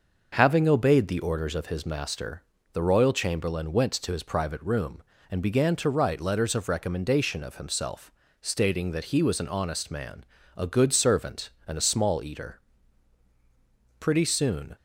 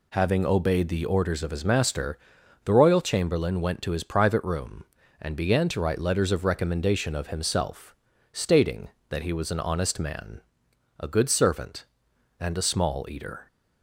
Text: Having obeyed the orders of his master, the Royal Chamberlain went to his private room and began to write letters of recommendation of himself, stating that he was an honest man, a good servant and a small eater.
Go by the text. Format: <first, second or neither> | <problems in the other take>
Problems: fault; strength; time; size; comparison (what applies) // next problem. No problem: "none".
second | starts louder than the rest; until 1.3 s; 6 dB // goes on to say "Pretty soon"; noticeable; from 13.9 s on; 0.76 s long